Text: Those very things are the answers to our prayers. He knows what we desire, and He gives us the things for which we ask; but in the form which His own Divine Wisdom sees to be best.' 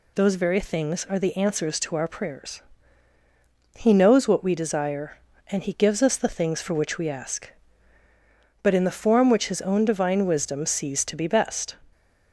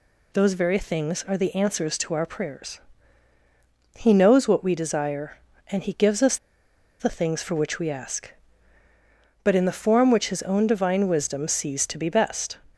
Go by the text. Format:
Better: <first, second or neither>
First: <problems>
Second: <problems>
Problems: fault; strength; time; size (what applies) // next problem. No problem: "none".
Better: first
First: none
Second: pauses between "us" and "the"; noticeable; at 6.3 s; 0.63 s long